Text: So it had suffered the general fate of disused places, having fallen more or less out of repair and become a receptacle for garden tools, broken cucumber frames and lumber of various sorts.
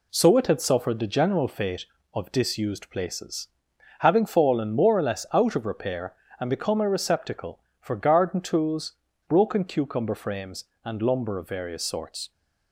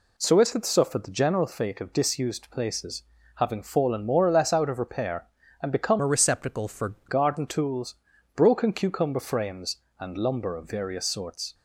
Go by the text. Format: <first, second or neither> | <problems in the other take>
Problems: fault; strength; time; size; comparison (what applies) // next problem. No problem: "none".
first | changes voice from "a" to "for"; from 6.0 to 6.9 s; 0.9 s long